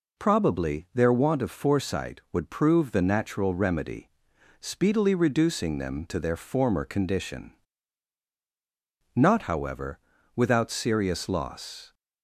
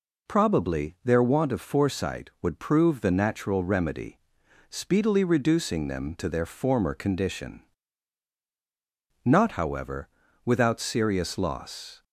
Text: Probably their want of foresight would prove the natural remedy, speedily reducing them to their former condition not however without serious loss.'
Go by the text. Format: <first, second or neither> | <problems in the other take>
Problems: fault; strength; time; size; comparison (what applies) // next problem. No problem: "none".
neither | pauses between "condition" and "not"; strong; the same in both // pauses between "however" and "without"; slight; the same in both